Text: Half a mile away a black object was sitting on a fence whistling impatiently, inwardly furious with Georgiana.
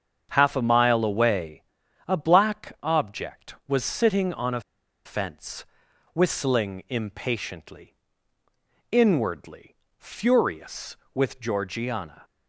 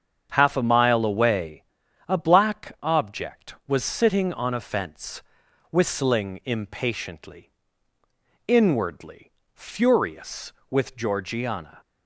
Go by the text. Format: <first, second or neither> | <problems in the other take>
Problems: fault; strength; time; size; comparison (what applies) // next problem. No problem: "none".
second | starts louder than the rest; strong; until 1.3 s; 7.5 dB; strong in the second // pauses between "away" and "a"; at 1.6 s; 0.44 s long; also in the second // pauses between "a" and "fence"; at 4.6 s; 0.45 s long // pauses between "fence" and "whistling"; noticeable; at 5.6 s; 0.50 s long; noticeable in the second // pauses between "inwardly" and "furious"; slight; at 9.7 s; 0.24 s long; slight in the second